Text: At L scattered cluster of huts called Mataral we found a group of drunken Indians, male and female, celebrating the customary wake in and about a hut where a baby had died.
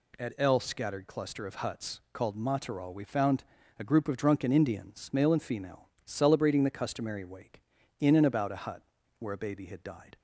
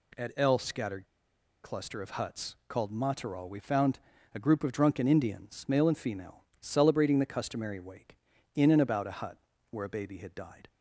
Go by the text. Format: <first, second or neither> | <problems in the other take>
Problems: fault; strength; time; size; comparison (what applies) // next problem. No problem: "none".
first | pauses between "scattered" and "cluster"; noticeable; at 1.0 s; 0.58 s long // pauses between "found" and "a"; slight; at 3.9 s; 0.36 s long; slight in the first // pauses between "hut" and "where"; slight; at 9.3 s; 0.34 s long; also in the first